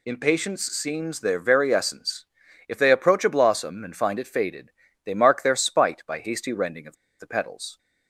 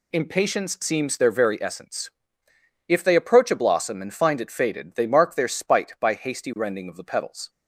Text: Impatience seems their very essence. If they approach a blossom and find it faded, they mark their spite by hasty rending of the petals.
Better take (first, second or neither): second